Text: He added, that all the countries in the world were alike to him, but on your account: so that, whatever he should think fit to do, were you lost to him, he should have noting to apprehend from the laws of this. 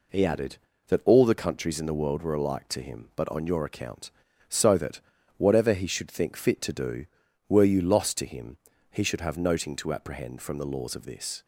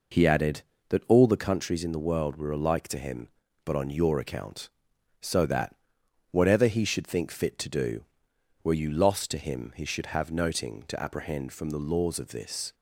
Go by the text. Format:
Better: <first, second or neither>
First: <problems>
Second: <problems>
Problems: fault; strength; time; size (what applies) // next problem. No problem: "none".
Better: neither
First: none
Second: none